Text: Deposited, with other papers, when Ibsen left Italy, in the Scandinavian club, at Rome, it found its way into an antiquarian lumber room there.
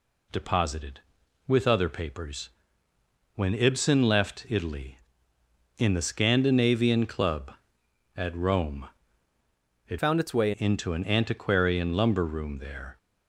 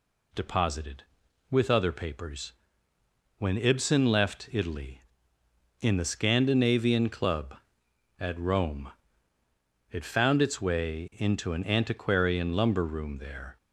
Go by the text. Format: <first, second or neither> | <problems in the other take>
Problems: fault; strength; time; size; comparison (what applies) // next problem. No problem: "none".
second | changes voice from "found" to "way"; from 9.9 to 10.5 s; 0.6 s long